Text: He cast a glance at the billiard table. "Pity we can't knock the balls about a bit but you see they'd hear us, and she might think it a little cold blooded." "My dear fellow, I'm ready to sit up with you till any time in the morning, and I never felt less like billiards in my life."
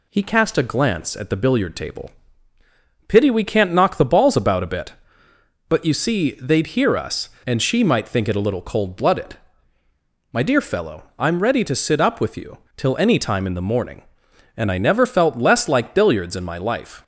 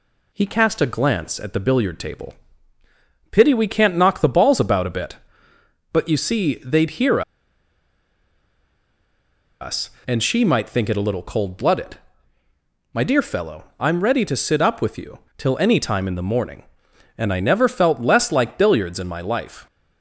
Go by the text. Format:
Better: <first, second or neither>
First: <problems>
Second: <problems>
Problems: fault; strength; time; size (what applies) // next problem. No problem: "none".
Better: first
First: pauses between "you" and "till"; slight; at 12.5 s; 0.18 s long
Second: pauses between "hear" and "us"; strong; at 7.2 s; 2.4 s long // pauses between "you" and "till"; slight; at 15.1 s; 0.18 s long